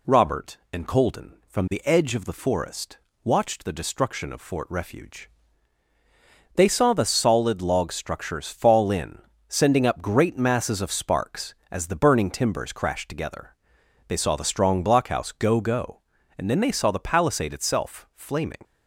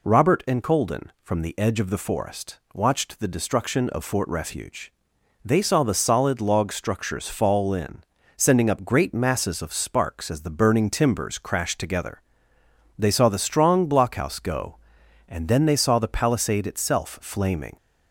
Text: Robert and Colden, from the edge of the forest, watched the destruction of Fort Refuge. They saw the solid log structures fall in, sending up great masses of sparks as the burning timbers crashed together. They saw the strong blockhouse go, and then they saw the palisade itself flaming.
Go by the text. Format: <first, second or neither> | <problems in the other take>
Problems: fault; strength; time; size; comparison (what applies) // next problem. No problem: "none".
second | says "go" twice; at 15.6 s